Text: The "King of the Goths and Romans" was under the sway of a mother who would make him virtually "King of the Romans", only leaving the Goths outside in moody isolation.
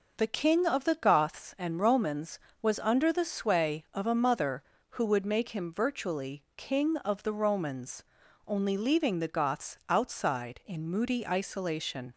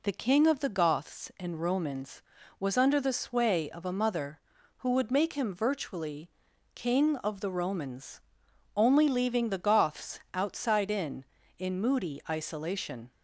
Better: first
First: none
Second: pauses between "virtually" and "King"; at 6.3 s; 0.44 s long // says "in" twice; at 11.5 s

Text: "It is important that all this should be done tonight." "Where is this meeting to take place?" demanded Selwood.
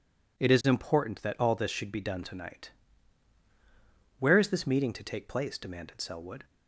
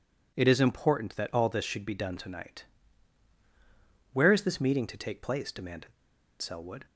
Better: first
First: none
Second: pauses between "demanded" and "Selwood"; noticeable; at 5.9 s; 0.47 s long

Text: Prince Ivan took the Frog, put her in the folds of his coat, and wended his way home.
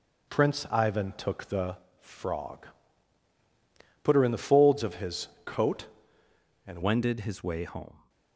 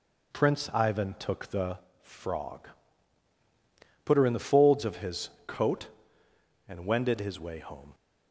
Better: second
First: pauses between "the" and "Frog"; slight; at 1.7 s; 0.24 s long // pauses between "his" and "coat"; slight; at 5.2 s; 0.16 s long // changes voice at "wended"; from 6.8 s on; 1.2 s long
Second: pauses between "the" and "Frog"; slight; at 1.7 s; 0.24 s long // pauses between "his" and "coat"; slight; at 5.3 s; 0.16 s long

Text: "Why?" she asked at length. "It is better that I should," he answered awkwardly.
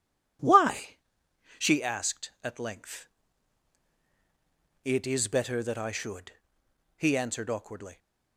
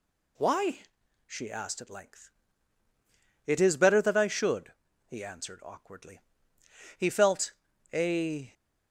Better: first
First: none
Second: goes on to say "He felt a"; from 6.9 s on; 1.5 s long

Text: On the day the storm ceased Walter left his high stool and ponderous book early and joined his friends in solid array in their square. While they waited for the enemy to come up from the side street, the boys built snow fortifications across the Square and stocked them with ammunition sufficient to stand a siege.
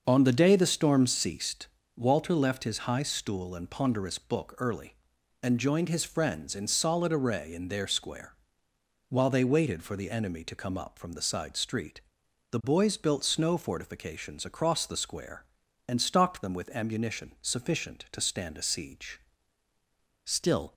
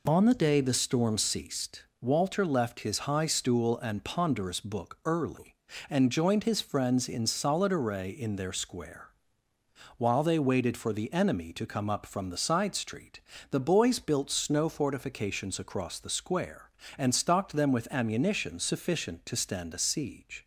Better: second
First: starts louder than the rest; noticeable; until 1.0 s; 6 dB // pauses between "ceased" and "Walter"; slight; at 1.6 s; 0.30 s long // goes on to say "Still"; from 20.2 s on; 0.50 s long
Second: pauses between "ceased" and "Walter"; slight; at 1.8 s; 0.18 s long

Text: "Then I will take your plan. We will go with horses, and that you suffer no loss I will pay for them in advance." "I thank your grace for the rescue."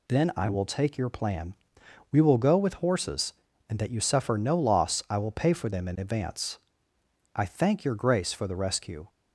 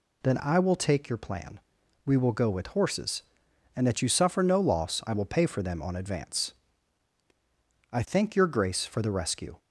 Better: first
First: none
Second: says "on" for "in"; at 5.8 s

